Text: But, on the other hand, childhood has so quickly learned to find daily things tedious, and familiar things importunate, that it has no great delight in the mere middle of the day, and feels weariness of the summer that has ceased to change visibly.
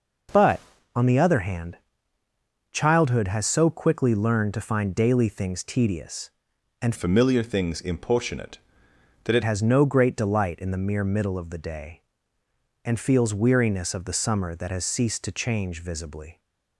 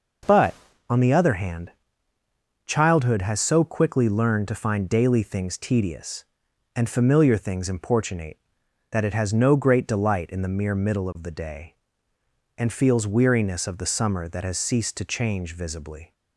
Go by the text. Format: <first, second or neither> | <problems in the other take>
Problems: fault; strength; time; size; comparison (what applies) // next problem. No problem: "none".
second | changes voice from "familiar" to "it"; from 6.9 to 9.4 s; 2.5 s long